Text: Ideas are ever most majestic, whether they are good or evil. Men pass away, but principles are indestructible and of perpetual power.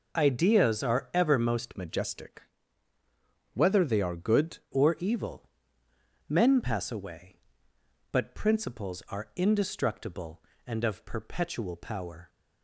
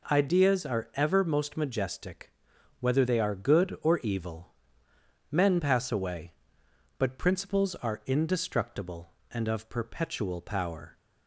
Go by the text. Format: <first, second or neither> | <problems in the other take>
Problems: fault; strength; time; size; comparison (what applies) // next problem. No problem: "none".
second | changes voice from "majestic" to "good"; from 1.7 to 4.5 s; 2.8 s long